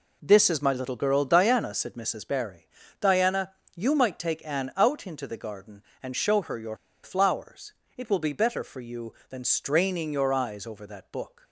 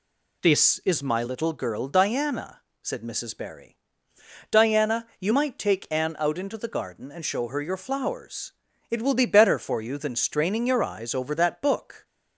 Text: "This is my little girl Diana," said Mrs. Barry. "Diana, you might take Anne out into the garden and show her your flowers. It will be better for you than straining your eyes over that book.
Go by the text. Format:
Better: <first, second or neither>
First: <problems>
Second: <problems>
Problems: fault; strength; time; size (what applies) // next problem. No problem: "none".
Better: second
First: pauses between "your" and "flowers"; slight; at 6.7 s; 0.26 s long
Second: none